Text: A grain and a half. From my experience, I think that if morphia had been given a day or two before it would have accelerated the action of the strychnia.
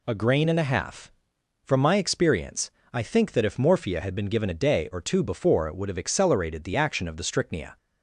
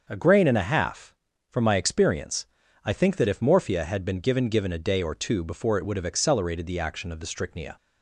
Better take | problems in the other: first | starts louder than the rest; until 1.0 s; 6.5 dB // says "given" twice; at 4.4 s

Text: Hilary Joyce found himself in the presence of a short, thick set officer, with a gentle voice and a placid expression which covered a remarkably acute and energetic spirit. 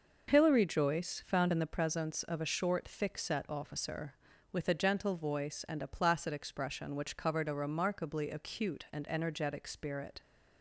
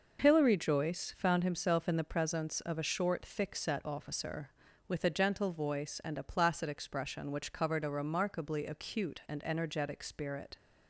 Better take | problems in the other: second | skips "himself"; at 1.5 s

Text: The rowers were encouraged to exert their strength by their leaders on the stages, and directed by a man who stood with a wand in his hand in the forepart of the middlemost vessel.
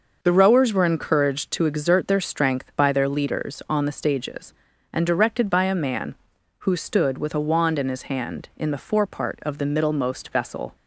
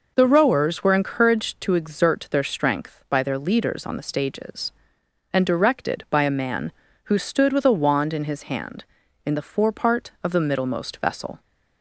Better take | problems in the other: neither | none

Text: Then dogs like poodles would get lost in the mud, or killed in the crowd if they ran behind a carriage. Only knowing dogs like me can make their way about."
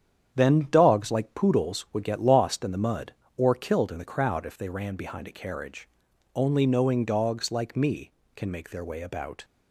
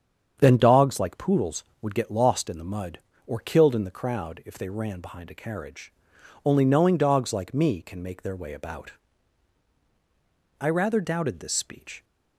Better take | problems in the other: first | starts louder than the rest; strong; until 1.4 s; 8 dB; strong in the first // goes on to say "I rather doubted this speech"; from 10.5 s on; 1.4 s long

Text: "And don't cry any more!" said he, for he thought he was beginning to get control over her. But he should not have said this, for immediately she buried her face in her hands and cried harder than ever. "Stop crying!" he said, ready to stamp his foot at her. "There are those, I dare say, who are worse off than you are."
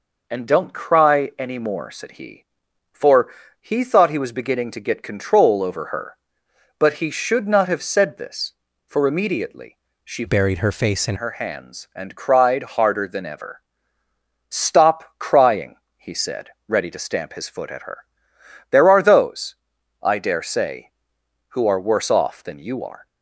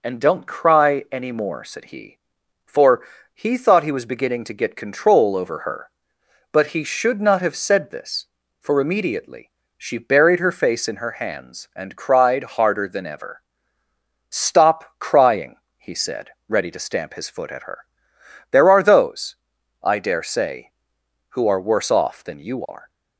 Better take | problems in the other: second | pauses between "for" and "he"; slight; at 3.2 s; 0.30 s long; slight in the second // pauses between "immediately" and "she"; slight; at 9.7 s; 0.26 s long; slight in the second // changes voice from "buried" to "in"; from 10.2 to 11.1 s; 0.9 s long

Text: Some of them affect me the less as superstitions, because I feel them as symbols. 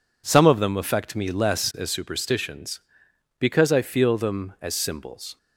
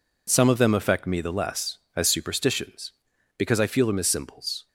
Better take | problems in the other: second | skips "the"; at 1.3 s

